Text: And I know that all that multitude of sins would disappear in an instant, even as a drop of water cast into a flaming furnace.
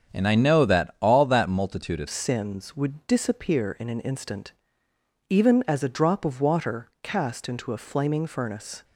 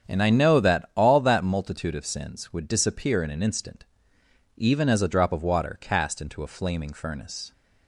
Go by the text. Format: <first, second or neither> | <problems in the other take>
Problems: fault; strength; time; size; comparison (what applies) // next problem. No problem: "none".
second | starts louder than the rest; strong; until 1.1 s; 7.5 dB; strong in the second // changes voice at "sins"; from 2.0 s on; 6.8 s long